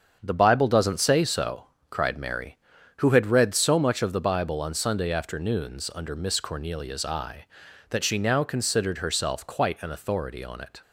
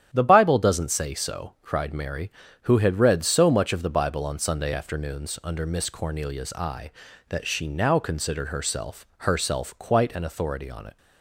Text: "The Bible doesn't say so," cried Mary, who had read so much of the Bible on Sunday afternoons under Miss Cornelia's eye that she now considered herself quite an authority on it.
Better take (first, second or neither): first